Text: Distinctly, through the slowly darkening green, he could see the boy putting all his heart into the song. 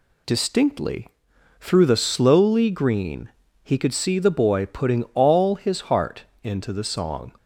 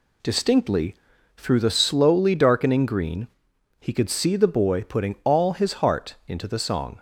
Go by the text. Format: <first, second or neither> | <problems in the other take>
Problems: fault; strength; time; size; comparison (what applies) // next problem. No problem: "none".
second | skips "darkening"; at 2.7 s // pauses between "heart" and "into"; slight; at 6.2 s; 0.20 s long